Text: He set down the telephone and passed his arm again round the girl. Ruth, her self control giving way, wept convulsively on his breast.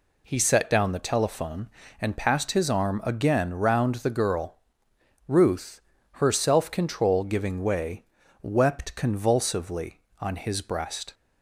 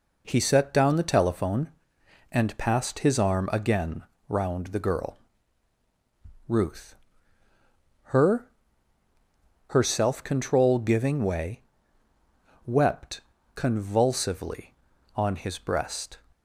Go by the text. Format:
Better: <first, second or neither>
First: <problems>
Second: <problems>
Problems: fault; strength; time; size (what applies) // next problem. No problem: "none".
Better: first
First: none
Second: pauses between "again" and "round"; slight; at 4.0 s; 0.26 s long // says "her" twice; at 9.6 s // pauses between "wept" and "convulsively"; slight; at 13.1 s; 0.34 s long